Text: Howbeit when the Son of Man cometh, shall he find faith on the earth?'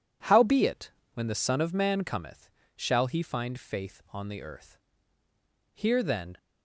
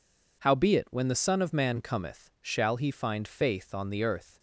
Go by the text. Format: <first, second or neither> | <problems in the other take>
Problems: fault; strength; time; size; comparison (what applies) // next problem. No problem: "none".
second | pauses between "Howbeit" and "when"; slight; at 0.9 s; 0.24 s long // goes on to say "Here then"; noticeable; from 5.7 s on; 0.64 s long